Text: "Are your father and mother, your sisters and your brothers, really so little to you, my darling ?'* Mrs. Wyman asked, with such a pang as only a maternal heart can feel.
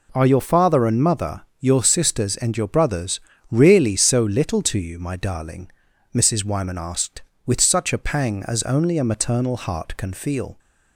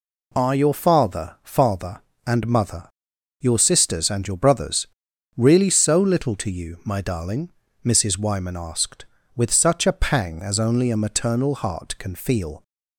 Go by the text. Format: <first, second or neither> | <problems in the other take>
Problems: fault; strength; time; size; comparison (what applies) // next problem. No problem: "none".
first | says "father" twice; at 1.4 s